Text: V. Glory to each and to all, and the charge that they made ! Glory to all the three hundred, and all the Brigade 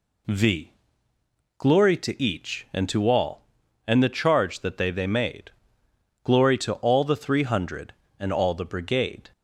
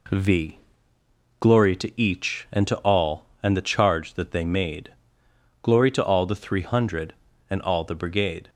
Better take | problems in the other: second | says "they" twice; at 4.9 s

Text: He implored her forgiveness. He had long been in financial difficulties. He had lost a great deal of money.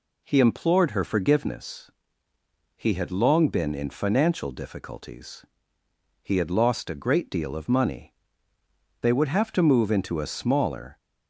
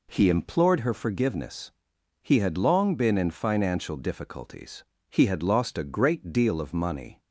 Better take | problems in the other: second | goes on to say "They would have to move into a smaller"; strong; from 9.0 s on; 1.9 s long

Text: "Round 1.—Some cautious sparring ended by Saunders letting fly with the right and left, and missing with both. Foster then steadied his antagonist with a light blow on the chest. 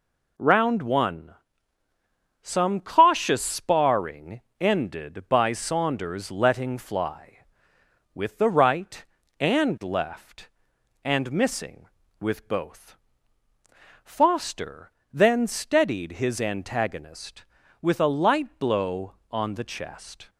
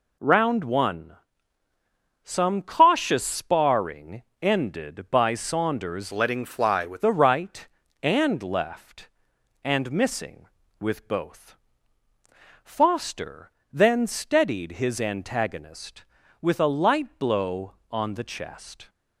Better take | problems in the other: first | pauses between "sparring" and "ended"; slight; at 4.2 s; 0.18 s long; slight in the first // changes voice from "letting" to "with"; from 6.1 to 7.0 s; 0.9 s long // pauses between "Foster" and "then"; slight; at 13.4 s; 0.24 s long; slight in the first

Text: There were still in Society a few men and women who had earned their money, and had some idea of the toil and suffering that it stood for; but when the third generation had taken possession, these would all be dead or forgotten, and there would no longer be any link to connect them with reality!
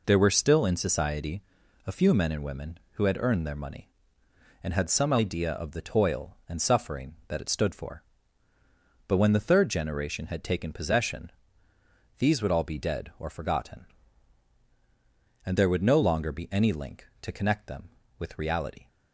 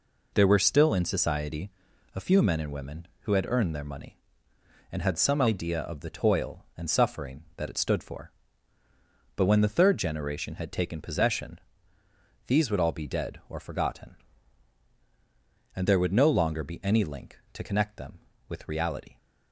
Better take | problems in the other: neither | pauses between "Society" and "a"; noticeable; the same in both

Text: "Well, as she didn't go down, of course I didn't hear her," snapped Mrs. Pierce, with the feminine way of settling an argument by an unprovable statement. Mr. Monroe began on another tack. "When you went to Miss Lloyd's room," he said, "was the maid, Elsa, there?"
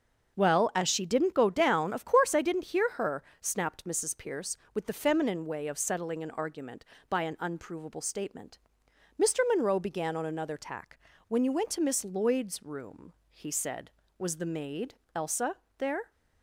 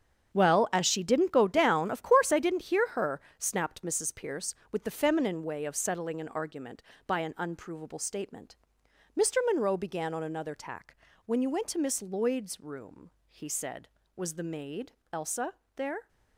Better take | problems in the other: first | gets quieter; strong; throughout; 11.5 dB // starts louder than the rest; strong; until 1.3 s; 7.5 dB; also in the first

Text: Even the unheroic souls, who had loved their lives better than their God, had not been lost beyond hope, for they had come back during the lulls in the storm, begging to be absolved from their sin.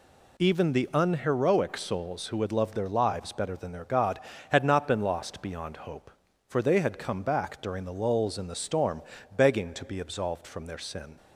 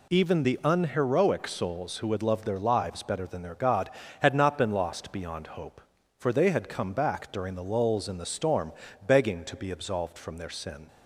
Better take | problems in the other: neither | none

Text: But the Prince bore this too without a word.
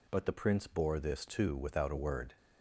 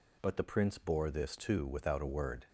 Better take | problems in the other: neither | none

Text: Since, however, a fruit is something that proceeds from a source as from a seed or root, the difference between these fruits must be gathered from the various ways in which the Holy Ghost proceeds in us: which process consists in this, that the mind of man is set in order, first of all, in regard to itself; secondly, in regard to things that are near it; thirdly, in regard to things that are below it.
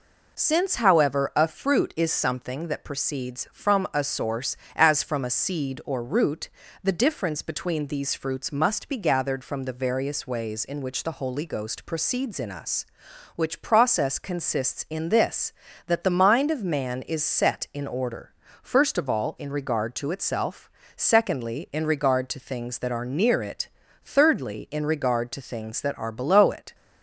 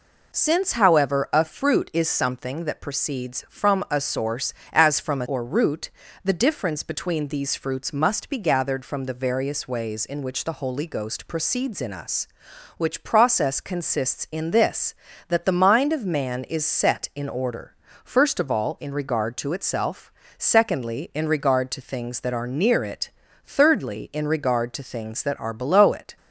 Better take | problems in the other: first | skips "seed"; at 5.2 s

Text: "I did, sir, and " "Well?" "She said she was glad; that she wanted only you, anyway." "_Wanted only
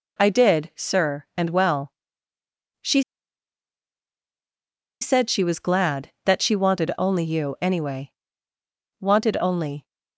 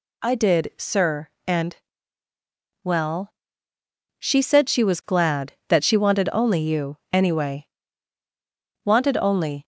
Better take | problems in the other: second | pauses between "She" and "said"; strong; at 3.0 s; 1.9 s long

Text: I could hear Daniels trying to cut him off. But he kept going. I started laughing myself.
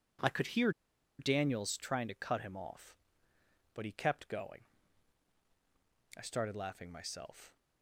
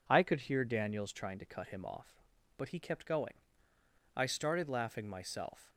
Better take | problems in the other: second | pauses between "hear" and "Daniels"; noticeable; at 0.6 s; 0.49 s long

